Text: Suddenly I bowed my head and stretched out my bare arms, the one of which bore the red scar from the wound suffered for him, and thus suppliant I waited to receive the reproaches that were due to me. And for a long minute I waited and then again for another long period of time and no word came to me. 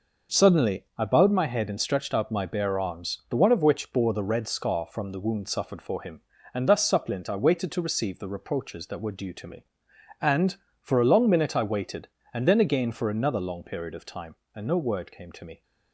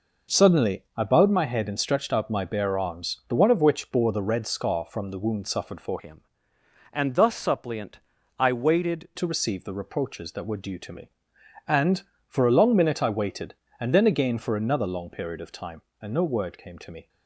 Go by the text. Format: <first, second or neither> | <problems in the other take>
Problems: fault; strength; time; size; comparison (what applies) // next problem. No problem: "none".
first | changes voice from "him" to "waited"; from 5.9 to 9.0 s; 3.1 s long // pauses between "suppliant" and "I"; at 8.0 s; 0.38 s long